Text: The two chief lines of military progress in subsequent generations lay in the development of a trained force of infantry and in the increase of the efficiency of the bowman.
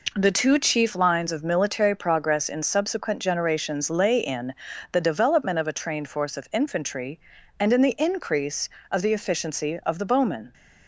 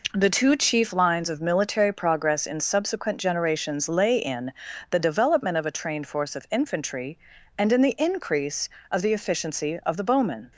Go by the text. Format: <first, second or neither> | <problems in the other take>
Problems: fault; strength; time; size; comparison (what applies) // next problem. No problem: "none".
neither | pauses between "in" and "the"; the same in both